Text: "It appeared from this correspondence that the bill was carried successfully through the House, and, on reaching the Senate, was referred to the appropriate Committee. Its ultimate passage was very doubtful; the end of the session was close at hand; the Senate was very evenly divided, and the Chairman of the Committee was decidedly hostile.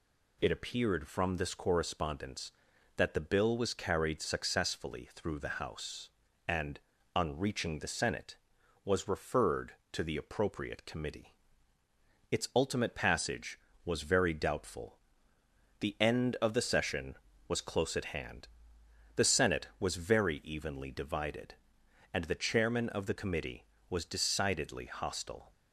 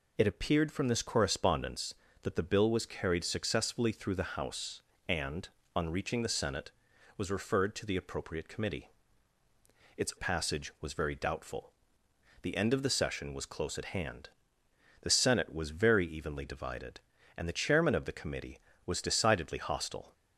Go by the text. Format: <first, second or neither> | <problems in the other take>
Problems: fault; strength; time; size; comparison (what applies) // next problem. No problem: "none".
first | skips "ultimate"; at 10.1 s